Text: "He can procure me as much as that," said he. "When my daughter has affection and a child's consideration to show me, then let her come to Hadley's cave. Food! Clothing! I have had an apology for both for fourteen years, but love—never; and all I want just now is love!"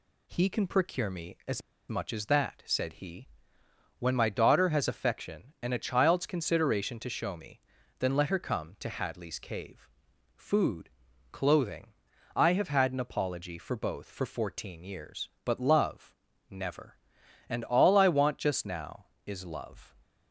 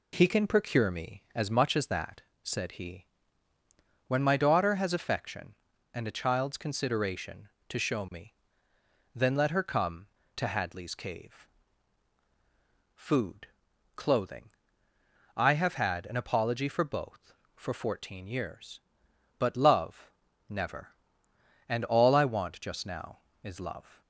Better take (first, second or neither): second